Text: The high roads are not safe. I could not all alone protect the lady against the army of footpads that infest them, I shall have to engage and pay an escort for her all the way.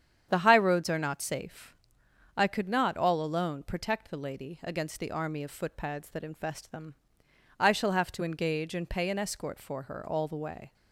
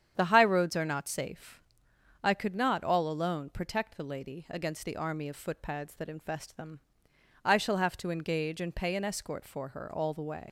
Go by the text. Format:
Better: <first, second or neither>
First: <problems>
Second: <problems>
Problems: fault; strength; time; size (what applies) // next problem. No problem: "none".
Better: first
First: starts louder than the rest; strong; until 1.3 s; 9 dB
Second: starts louder than the rest; strong; until 1.1 s; 9 dB // leaves "way" unfinished; at 10.4 s; 95 ms